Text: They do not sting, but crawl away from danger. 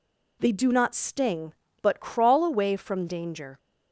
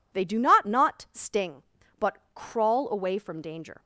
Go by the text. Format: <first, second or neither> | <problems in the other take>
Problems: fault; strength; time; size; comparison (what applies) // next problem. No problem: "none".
first | says "not" twice; at 0.6 s // pauses between "but" and "crawl"; slight; at 2.1 s; 0.18 s long